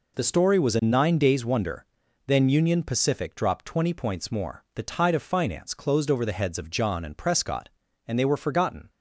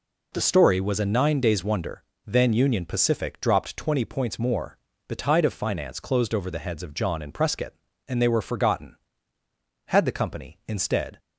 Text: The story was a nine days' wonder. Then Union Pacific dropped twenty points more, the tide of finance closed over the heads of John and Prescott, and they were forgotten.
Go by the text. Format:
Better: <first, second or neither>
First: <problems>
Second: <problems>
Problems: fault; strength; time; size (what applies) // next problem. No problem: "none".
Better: first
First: none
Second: goes on to say "Had the company instead"; noticeable; from 9.8 s on; 1.3 s long